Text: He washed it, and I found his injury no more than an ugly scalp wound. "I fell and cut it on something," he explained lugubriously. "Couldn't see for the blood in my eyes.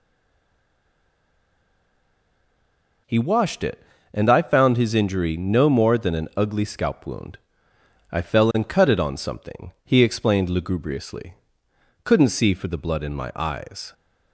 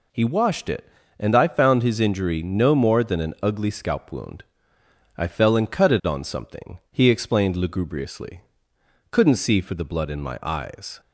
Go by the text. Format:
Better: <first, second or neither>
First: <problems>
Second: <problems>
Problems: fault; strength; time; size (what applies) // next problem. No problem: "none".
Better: second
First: stays silent before the first word; strong; until 3.0 s; 3.0 s long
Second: none